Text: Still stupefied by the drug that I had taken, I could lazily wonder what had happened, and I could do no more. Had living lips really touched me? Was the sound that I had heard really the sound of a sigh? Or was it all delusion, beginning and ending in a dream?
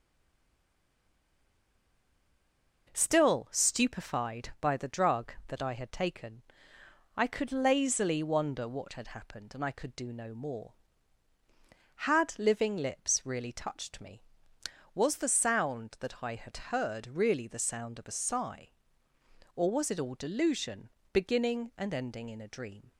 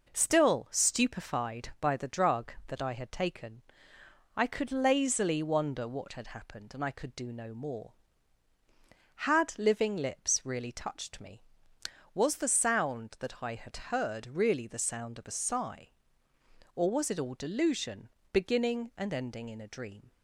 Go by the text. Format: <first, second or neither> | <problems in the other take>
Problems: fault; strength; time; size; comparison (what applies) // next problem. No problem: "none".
second | stays silent before the first word; strong; until 2.8 s; 2.8 s long